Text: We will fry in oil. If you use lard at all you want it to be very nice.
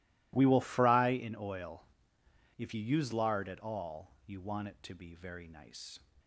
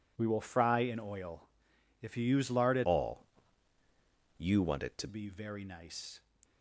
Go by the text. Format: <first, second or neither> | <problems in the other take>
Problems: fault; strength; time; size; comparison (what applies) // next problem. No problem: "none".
first | changes voice from "all" to "to"; from 2.8 to 5.0 s; 2.2 s long // pauses between "all" and "you"; at 3.2 s; 1.1 s long